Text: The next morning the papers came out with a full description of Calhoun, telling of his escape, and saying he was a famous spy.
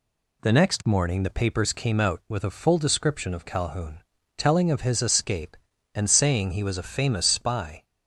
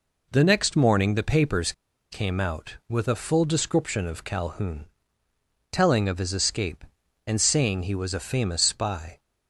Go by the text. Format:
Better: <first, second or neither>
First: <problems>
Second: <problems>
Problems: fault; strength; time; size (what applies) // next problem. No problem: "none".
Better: first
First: none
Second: pauses between "papers" and "came"; at 1.7 s; 0.39 s long